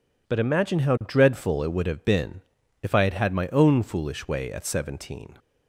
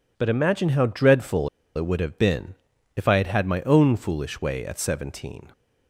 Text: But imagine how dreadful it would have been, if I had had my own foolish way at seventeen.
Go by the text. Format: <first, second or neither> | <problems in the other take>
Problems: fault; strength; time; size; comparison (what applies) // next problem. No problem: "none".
first | pauses between "dreadful" and "it"; slight; at 1.4 s; 0.27 s long